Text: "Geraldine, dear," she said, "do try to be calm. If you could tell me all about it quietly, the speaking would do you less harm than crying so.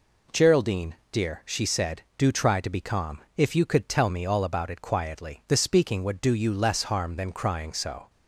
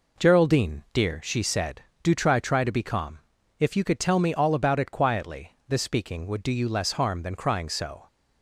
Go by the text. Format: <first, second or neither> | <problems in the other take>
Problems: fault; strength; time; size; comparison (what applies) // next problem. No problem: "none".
first | says "try" twice; at 2.3 s